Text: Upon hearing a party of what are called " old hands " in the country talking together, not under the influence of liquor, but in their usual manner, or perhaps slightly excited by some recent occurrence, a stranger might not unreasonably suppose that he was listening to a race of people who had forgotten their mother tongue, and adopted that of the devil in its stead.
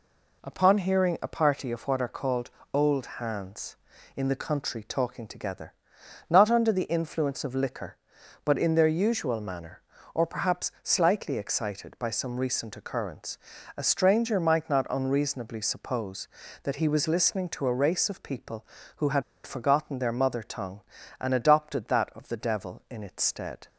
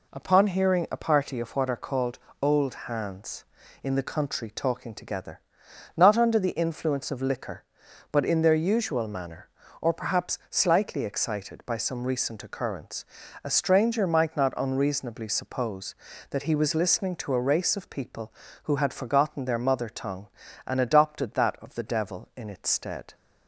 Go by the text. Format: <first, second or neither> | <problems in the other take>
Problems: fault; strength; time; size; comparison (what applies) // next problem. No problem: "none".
second | pauses between "had" and "forgotten"; slight; at 19.2 s; 0.23 s long